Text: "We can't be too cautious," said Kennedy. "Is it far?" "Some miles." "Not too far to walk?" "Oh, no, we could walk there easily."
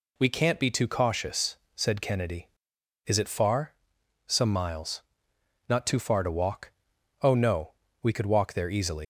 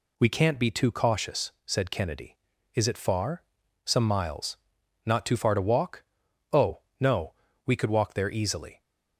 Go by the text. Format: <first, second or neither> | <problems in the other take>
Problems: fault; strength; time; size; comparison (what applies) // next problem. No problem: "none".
second | leaves "easily" unfinished; at 9.0 s; 125 ms